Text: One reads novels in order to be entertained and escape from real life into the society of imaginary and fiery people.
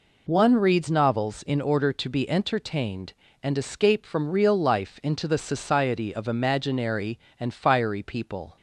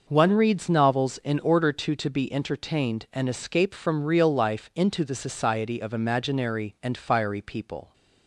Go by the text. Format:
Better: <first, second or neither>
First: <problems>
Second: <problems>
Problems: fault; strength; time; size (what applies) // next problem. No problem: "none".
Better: first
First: none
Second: says "to" twice; at 1.9 s